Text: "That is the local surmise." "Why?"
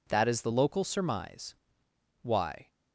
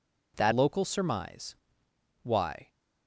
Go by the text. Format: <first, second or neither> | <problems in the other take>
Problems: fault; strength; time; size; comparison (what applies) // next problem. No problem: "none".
first | skips "is the"; at 0.5 s